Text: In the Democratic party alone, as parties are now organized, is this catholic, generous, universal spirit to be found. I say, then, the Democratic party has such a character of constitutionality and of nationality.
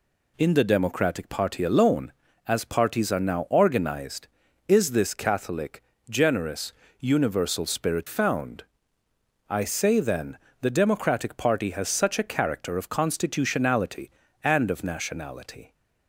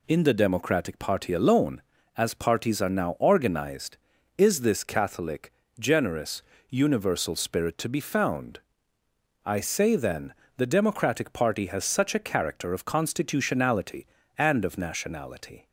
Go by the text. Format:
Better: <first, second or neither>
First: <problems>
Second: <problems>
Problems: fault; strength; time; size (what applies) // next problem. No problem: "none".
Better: second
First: skips "to be"; at 8.0 s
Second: none